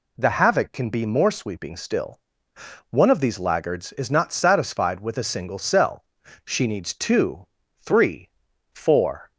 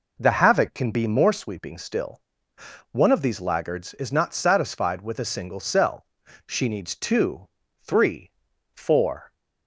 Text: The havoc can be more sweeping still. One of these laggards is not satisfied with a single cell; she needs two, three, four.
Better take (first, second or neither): first